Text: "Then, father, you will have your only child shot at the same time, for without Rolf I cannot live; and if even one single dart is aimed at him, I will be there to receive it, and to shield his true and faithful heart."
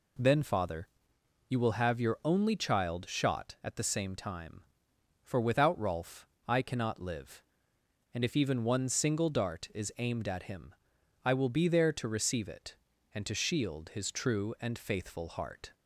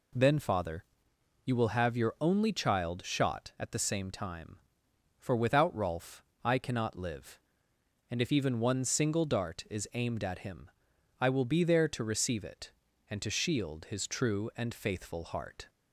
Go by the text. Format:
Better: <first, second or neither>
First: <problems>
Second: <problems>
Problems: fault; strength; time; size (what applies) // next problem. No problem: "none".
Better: neither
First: pauses between "Rolf" and "I"; slight; at 6.2 s; 0.22 s long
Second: pauses between "Rolf" and "I"; slight; at 6.2 s; 0.22 s long